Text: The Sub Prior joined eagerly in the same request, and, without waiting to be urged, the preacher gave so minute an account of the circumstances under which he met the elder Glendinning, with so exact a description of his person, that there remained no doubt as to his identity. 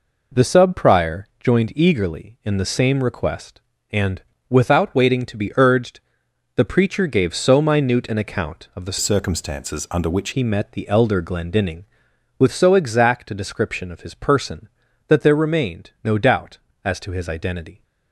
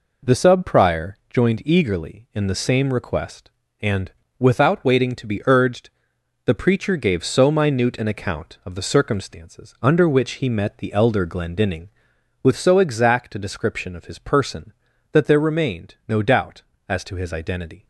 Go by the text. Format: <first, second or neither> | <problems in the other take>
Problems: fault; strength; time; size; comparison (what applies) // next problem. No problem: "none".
second | changes voice from "circumstances" to "which"; from 8.9 to 10.2 s; 1.3 s long